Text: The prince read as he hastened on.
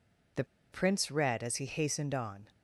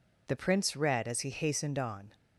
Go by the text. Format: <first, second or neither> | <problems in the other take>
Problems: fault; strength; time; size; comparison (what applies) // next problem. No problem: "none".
second | pauses between "The" and "prince"; slight; at 0.4 s; 0.27 s long